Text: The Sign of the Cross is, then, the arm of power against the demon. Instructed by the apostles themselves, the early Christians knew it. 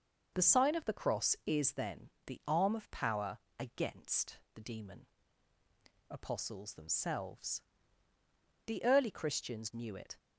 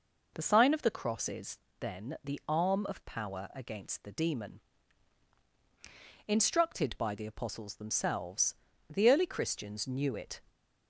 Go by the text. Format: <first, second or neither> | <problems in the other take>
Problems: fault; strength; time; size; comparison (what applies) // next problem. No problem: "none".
second | pauses between "power" and "against"; slight; at 3.3 s; 0.22 s long // pauses between "against" and "the"; slight; at 4.3 s; 0.16 s long // skips "Instructed by the"; at 5.5 s